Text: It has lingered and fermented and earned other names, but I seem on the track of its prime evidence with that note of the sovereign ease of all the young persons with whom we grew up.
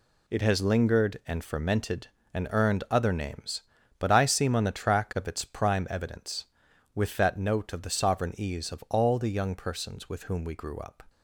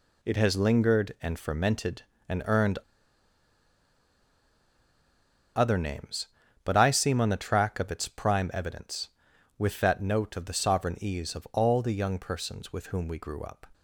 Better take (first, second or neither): first